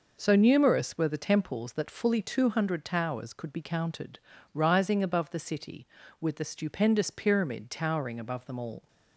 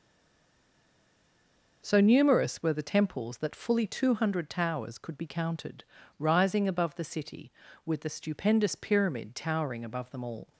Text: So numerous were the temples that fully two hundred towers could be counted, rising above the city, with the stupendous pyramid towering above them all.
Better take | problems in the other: first | stays silent before the first word; noticeable; until 1.8 s; 1.8 s long

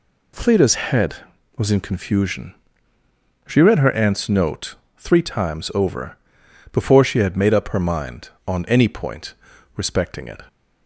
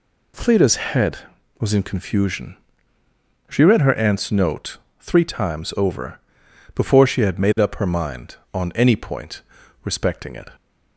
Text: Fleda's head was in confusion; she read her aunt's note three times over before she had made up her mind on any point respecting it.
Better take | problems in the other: neither | pauses between "note" and "three"; slight; the same in both // pauses between "over" and "before"; noticeable; the same in both // pauses between "point" and "respecting"; the same in both

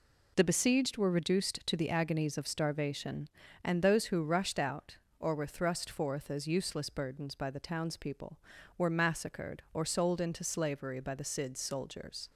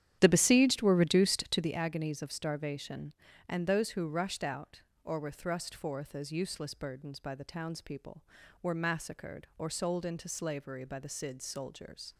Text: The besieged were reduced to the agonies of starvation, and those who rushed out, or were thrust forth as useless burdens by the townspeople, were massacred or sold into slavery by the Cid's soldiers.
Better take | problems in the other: first | starts louder than the rest; strong; until 1.8 s; 10.5 dB

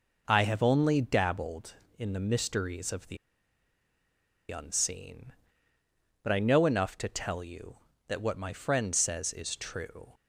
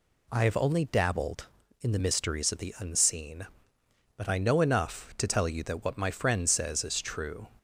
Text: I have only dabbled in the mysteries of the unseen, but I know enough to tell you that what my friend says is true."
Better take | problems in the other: second | pauses between "the" and "unseen"; strong; at 3.1 s; 1.3 s long

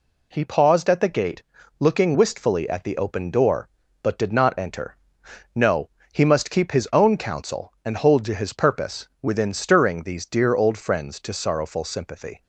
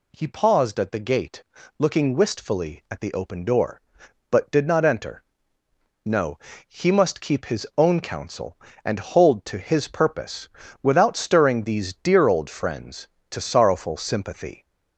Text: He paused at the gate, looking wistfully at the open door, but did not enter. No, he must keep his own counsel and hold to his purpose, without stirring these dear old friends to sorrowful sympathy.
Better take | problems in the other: second | says "within" for "without"; at 9.2 s

